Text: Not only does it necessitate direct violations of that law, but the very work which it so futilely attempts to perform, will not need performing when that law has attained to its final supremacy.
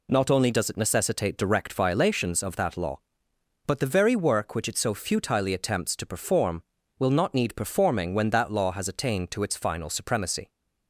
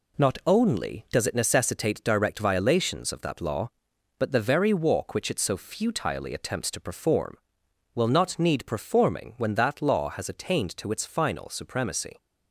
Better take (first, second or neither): first